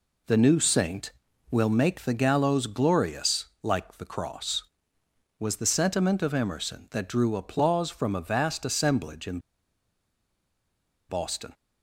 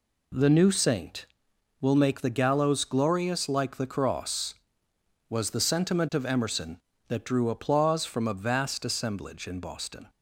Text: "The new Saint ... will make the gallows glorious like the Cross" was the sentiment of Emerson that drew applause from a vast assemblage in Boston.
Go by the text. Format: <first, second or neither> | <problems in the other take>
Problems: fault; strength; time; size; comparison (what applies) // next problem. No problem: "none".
second | pauses between "glorious" and "like"; slight; at 3.4 s; 0.18 s long // pauses between "in" and "Boston"; strong; at 9.3 s; 1.7 s long